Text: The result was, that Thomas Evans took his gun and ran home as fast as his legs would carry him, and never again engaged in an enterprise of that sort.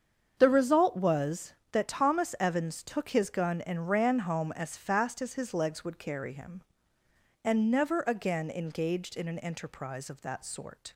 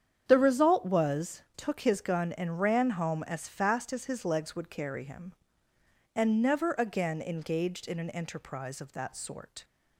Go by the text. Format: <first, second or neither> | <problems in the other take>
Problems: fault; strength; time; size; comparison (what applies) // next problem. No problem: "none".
first | starts louder than the rest; strong; until 1.2 s; 8.5 dB; strong in the first // skips "that Thomas Evans"; at 1.4 s